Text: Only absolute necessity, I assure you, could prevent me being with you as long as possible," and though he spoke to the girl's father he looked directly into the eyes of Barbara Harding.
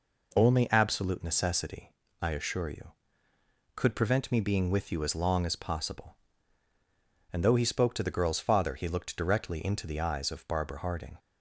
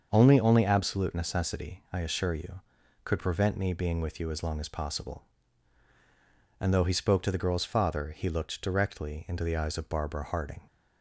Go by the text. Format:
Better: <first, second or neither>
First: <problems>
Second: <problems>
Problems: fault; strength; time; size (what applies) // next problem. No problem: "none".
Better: first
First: none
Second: starts louder than the rest; until 1.1 s; 6.5 dB // says "Only" twice; at 0.3 s